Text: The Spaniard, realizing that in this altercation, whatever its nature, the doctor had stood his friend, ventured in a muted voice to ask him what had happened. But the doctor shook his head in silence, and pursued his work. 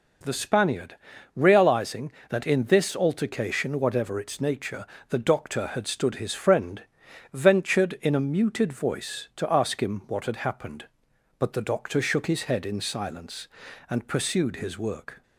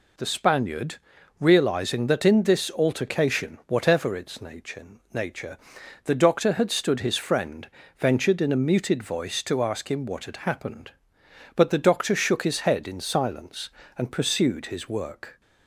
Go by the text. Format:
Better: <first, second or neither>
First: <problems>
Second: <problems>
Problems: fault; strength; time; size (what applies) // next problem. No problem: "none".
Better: first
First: none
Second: says "nature" twice; at 5.1 s